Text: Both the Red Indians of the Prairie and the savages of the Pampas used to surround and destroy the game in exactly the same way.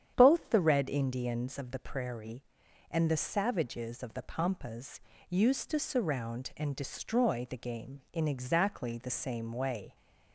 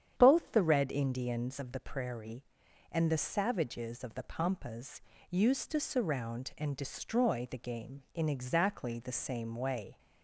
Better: neither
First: starts louder than the rest; strong; until 1.1 s; 9 dB // pauses between "Pampas" and "used"; slight; at 5.0 s; 0.28 s long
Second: starts louder than the rest; strong; until 1.1 s; 9 dB // pauses between "Pampas" and "used"; slight; at 5.0 s; 0.28 s long

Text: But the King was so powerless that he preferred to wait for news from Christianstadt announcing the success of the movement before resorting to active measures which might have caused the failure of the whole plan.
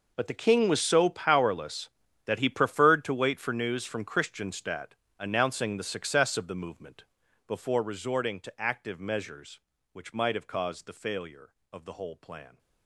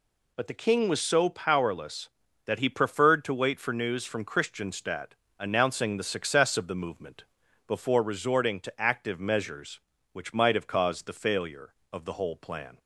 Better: second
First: gets quieter; strong; throughout; 17.5 dB // pauses between "Christianstadt" and "announcing"; slight; at 4.9 s; 0.26 s long // pauses between "movement" and "before"; at 7.0 s; 0.42 s long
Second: pauses between "Christianstadt" and "announcing"; slight; at 5.1 s; 0.26 s long // pauses between "movement" and "before"; at 7.2 s; 0.42 s long

